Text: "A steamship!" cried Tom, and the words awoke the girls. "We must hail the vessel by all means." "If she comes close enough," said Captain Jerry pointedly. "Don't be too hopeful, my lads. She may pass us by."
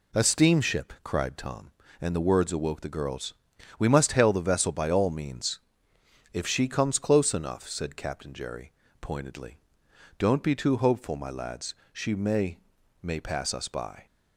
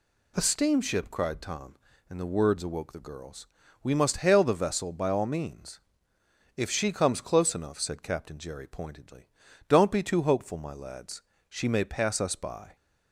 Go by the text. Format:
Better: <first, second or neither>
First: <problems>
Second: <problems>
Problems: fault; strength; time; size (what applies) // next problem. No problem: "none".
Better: second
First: pauses between "Jerry" and "pointedly"; slight; at 8.7 s; 0.28 s long // says "may" twice; at 13.0 s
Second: none